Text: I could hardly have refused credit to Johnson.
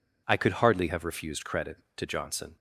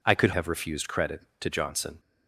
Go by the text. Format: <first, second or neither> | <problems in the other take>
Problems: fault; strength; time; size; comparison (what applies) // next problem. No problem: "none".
first | skips "hardly"; at 0.3 s